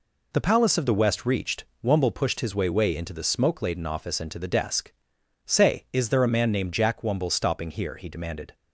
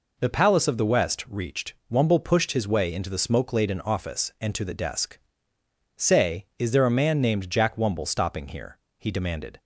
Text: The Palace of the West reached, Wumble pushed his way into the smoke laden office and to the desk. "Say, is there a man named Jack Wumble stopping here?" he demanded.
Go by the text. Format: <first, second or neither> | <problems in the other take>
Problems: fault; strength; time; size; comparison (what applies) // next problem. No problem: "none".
second | says "way" twice; at 2.7 s